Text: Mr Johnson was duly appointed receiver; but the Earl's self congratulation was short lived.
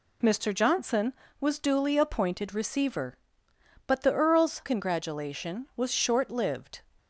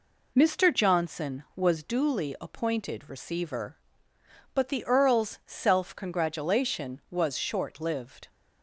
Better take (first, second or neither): second